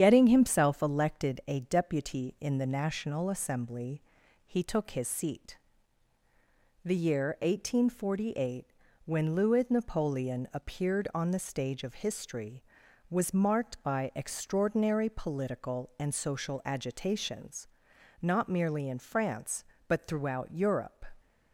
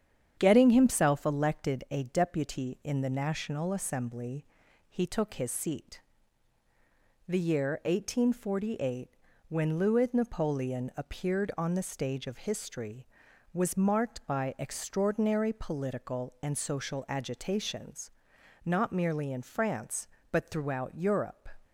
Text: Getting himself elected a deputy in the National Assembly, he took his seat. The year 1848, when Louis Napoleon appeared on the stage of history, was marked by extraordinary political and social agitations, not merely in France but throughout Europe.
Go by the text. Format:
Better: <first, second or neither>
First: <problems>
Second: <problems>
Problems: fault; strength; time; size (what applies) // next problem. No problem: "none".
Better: second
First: loses the start of "Getting"; at 0.0 s; 65 ms // starts louder than the rest; strong; until 1.0 s; 8.5 dB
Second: starts louder than the rest; strong; until 1.3 s; 8.5 dB